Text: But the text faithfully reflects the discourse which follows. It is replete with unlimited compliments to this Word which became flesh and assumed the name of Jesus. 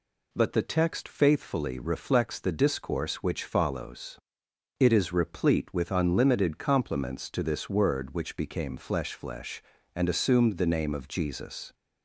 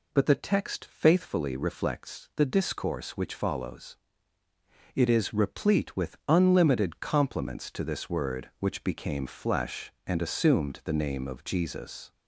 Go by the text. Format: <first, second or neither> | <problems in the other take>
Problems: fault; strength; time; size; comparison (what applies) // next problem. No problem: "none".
second | says "flesh" twice; at 9.1 s